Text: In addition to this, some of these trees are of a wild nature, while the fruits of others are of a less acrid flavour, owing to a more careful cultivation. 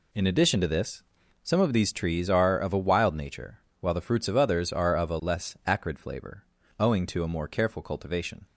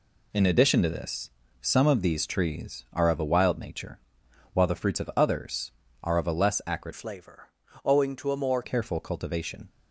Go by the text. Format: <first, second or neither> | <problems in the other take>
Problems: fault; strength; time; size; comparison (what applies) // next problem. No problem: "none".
first | changes voice from "flavour" to "more"; from 6.9 to 8.6 s; 1.7 s long